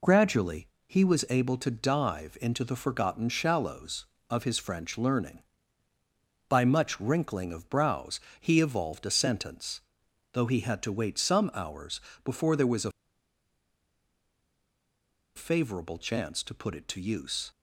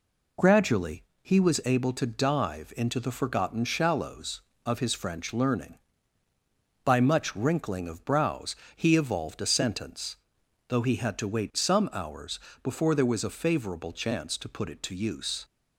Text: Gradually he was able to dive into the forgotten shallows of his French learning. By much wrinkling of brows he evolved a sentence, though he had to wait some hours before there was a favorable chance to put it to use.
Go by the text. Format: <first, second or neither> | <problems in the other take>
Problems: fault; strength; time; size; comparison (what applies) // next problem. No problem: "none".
second | pauses between "Gradually" and "he"; slight; at 0.6 s; 0.18 s long; slight in the second // pauses between "brows" and "he"; slight; at 8.1 s; 0.18 s long; slight in the second // pauses between "hours" and "before"; slight; at 12.0 s; 0.24 s long; slight in the second // pauses between "a" and "favorable"; strong; at 12.9 s; 2.4 s long